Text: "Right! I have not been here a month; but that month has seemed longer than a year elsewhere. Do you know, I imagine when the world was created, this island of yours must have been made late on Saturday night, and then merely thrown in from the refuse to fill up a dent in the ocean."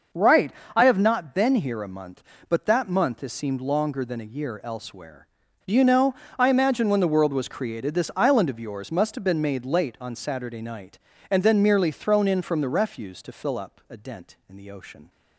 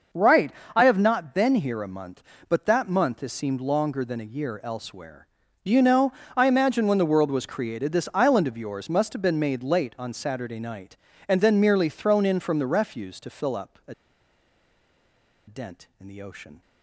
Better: first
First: none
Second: pauses between "a" and "dent"; strong; at 13.9 s; 1.5 s long

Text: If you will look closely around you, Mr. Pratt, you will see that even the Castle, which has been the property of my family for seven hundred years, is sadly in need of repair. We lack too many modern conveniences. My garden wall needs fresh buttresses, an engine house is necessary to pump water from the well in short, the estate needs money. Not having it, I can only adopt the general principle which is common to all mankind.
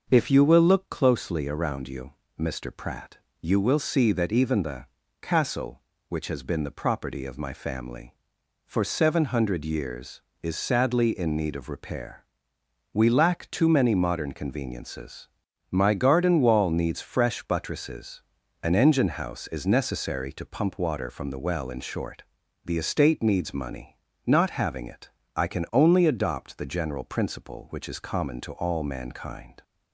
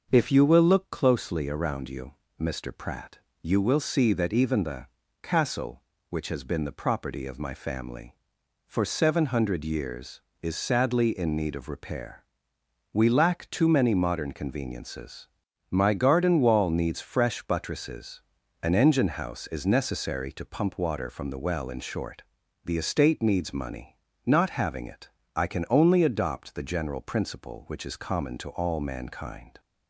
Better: neither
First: starts louder than the rest; until 1.1 s; 6.5 dB // pauses between "the" and "Castle"; slight; at 4.8 s; 0.34 s long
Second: starts louder than the rest; until 1.1 s; 6.5 dB // pauses between "the" and "Castle"; slight; at 4.8 s; 0.34 s long

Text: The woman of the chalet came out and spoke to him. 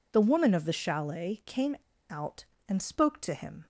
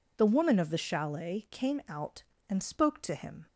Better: second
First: pauses between "came" and "out"; slight; at 1.7 s; 0.34 s long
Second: none

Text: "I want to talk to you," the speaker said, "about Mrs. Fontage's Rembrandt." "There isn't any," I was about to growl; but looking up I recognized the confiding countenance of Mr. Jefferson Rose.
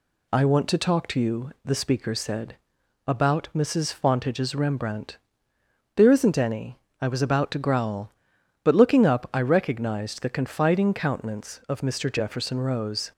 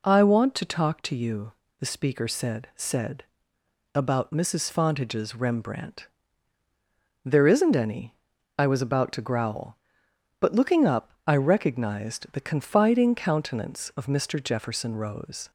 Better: first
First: none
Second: says "said" twice; at 2.7 s // pauses between "up" and "I"; slight; at 11.1 s; 0.16 s long

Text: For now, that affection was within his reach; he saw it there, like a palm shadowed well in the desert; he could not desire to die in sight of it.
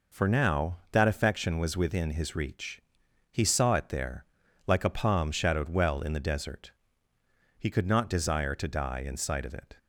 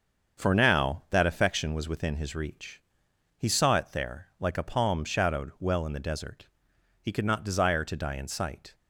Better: first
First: none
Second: starts louder than the rest; until 1.4 s; 7 dB // stops before "of it"; at 8.7 s

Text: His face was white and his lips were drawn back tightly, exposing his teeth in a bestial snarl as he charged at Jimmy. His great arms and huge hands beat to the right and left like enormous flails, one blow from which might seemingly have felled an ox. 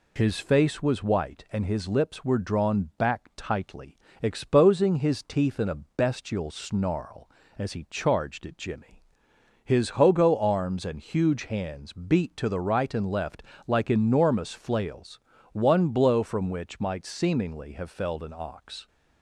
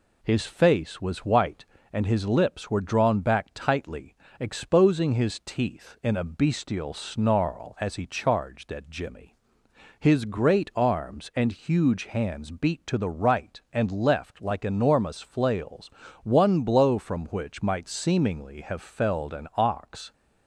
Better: second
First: says "hogo" for "great"; at 9.9 s // pauses between "left" and "like"; slight; at 13.4 s; 0.24 s long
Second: none

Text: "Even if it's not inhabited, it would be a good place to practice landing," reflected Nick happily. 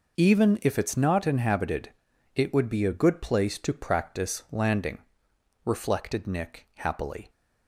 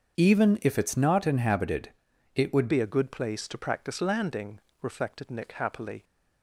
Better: first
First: none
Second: starts louder than the rest; until 1.2 s; 7 dB // changes voice at "be"; from 2.6 s on; 3.4 s long

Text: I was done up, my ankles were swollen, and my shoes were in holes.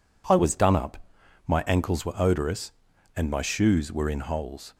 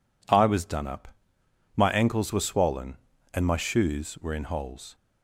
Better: second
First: says "odorous" for "swollen"; at 2.1 s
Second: none

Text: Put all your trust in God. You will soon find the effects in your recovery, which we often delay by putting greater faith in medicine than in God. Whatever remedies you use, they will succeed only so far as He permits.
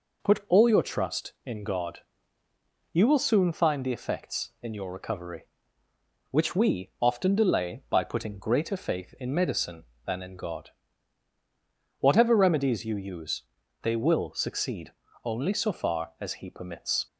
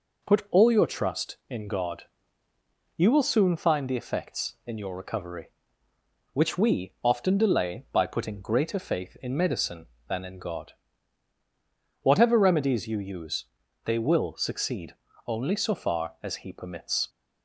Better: neither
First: pauses between "succeed" and "only"; slight; at 14.9 s; 0.34 s long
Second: pauses between "succeed" and "only"; slight; at 14.9 s; 0.34 s long

